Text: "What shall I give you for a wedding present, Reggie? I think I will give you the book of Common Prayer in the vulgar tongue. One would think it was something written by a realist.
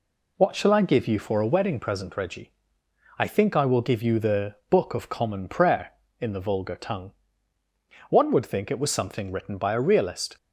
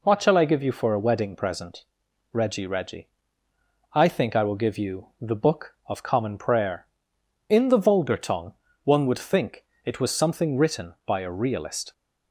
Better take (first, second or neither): first